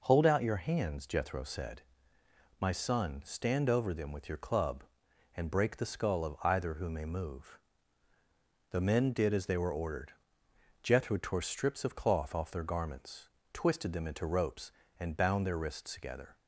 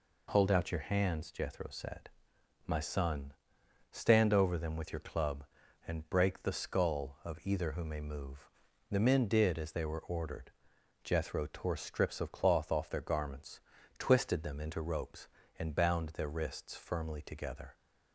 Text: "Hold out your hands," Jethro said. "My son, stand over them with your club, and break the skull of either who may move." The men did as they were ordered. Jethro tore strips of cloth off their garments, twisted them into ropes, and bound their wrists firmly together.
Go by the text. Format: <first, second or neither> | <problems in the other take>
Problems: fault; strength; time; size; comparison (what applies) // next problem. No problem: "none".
second | skips "firmly"; at 15.9 s